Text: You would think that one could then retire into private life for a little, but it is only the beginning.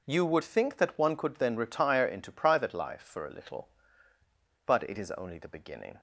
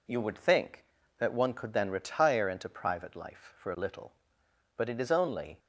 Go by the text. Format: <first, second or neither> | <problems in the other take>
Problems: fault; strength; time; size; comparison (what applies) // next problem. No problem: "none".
first | stops before "the beginning"; at 5.5 s